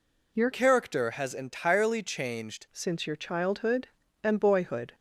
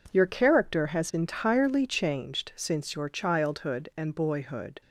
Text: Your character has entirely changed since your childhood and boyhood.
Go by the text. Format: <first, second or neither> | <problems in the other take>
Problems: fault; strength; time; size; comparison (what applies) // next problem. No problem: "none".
second | changes voice from "character" to "changed"; from 0.5 to 2.6 s; 2.1 s long